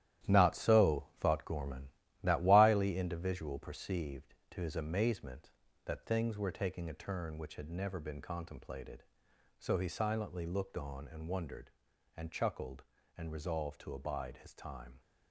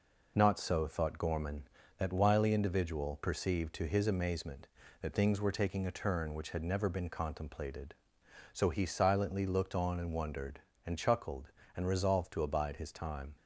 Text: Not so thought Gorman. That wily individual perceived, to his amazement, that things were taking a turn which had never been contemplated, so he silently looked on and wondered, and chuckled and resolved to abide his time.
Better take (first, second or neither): second